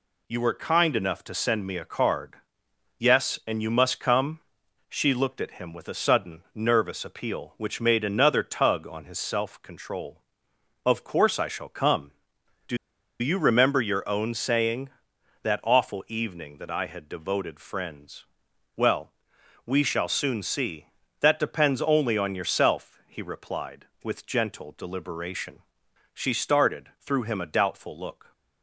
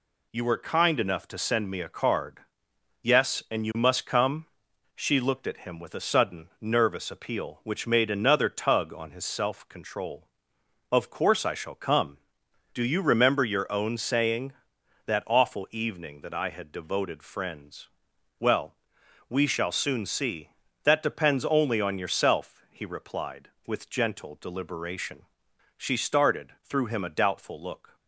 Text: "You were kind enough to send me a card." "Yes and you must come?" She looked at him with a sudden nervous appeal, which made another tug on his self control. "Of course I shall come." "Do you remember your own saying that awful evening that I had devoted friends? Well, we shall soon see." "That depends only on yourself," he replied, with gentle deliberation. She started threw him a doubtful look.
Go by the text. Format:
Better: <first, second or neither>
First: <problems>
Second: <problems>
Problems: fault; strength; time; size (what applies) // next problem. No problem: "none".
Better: second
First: pauses between "Do" and "you"; at 12.7 s; 0.43 s long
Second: none